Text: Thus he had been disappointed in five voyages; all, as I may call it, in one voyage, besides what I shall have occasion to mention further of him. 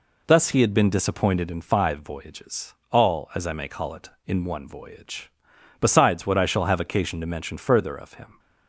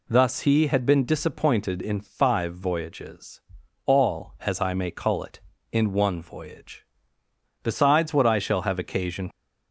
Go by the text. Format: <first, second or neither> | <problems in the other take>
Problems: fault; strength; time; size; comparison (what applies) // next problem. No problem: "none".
first | stops before "to mention further of him"; at 9.3 s